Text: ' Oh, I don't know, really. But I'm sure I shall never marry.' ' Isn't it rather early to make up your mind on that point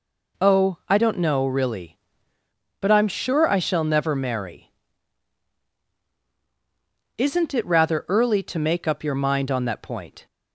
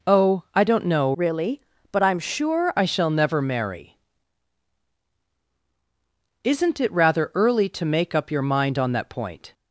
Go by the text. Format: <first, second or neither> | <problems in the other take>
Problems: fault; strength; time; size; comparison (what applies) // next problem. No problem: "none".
first | changes voice from "really" to "sure"; from 1.1 to 2.7 s; 1.6 s long